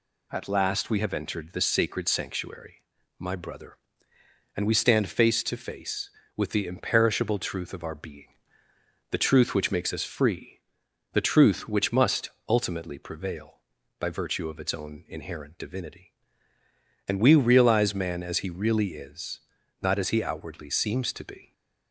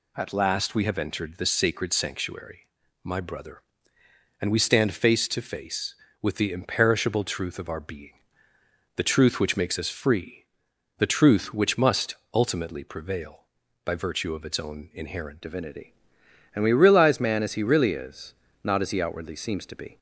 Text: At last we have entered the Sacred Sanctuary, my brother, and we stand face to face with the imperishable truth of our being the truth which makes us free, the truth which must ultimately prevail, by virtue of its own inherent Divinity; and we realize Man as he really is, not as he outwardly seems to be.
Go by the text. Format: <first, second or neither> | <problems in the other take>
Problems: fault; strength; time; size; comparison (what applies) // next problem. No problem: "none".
first | pauses between "being" and "the"; noticeable; at 8.1 s; 0.84 s long; noticeable in the first // pauses between "must" and "ultimately"; slight; at 12.1 s; 0.20 s long; slight in the first // changes voice at "Divinity"; from 15.4 s on; 4.5 s long